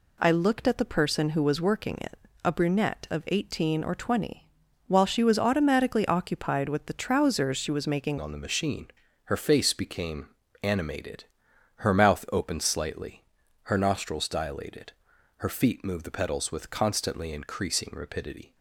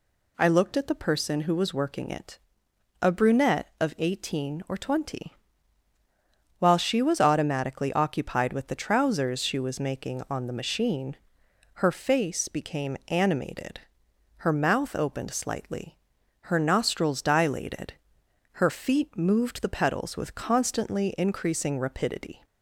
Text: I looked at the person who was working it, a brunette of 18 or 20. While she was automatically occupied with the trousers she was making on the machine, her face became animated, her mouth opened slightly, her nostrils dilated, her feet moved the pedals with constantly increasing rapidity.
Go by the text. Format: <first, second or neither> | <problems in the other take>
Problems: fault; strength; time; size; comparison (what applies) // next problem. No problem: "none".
second | changes voice at "on"; from 8.1 s on; 10.4 s long // pauses between "became" and "animated"; slight; at 10.2 s; 0.34 s long